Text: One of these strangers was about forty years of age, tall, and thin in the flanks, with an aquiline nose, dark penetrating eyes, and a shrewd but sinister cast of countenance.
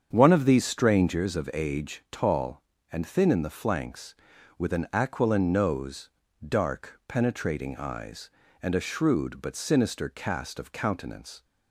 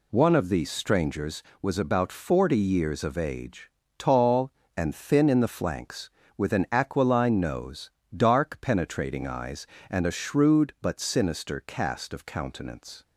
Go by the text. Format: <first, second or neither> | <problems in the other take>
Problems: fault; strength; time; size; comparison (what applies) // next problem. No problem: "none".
second | starts louder than the rest; strong; until 1.1 s; 7.5 dB // skips "was about forty years"; at 1.3 s